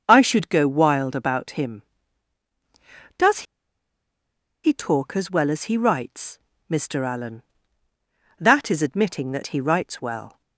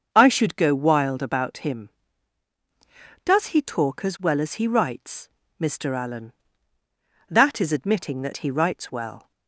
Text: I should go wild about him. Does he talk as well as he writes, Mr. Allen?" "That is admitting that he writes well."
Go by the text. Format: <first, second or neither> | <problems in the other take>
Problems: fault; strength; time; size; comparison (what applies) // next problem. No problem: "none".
second | starts louder than the rest; until 1.0 s; 6.5 dB; also in the second // pauses between "Does" and "he"; at 3.4 s; 1.2 s long